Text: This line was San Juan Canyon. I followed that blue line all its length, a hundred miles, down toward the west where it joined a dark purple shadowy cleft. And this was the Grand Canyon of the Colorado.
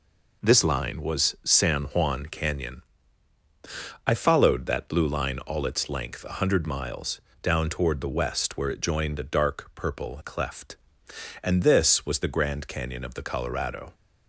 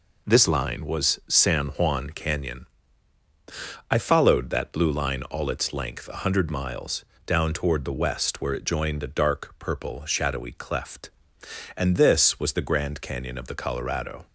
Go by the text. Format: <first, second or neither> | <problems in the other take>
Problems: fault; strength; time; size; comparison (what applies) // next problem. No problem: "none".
second | skips "shadowy"; at 10.2 s